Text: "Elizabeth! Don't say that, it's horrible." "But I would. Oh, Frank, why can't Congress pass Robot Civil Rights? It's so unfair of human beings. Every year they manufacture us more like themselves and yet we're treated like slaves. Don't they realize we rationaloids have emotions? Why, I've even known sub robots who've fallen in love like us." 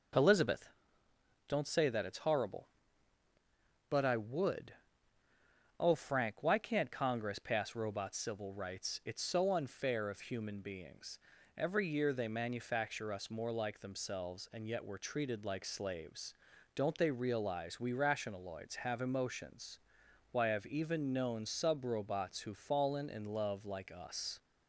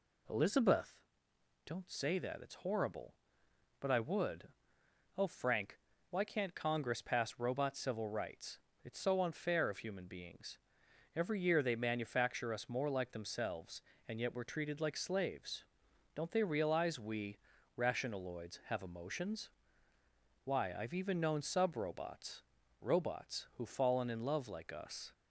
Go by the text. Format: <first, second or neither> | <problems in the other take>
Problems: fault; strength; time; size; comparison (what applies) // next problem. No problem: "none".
first | pauses between "we" and "rationaloids"; at 17.3 s; 0.42 s long // says "robots" twice; at 22.7 s